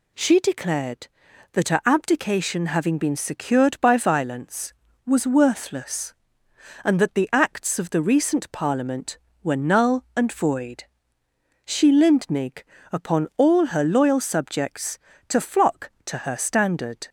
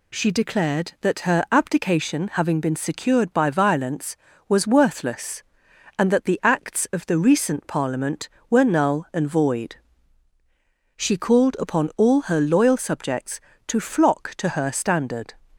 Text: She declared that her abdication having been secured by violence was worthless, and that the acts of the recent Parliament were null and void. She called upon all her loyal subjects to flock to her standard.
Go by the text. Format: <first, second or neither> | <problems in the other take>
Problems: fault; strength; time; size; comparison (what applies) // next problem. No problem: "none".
second | says "lindnig" for "called"; at 11.9 s